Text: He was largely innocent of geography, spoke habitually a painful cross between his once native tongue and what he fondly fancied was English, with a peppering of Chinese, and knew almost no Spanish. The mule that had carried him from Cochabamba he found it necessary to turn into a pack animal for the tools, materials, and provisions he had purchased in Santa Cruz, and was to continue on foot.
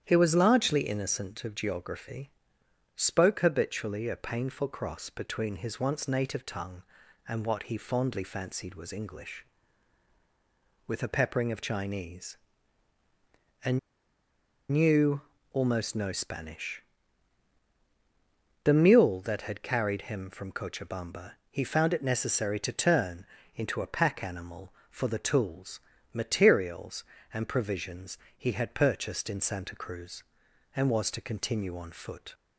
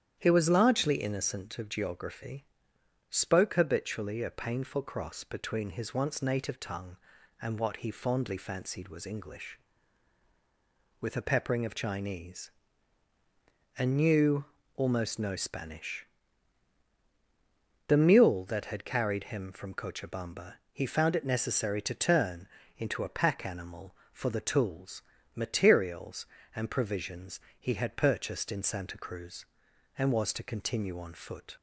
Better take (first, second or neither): second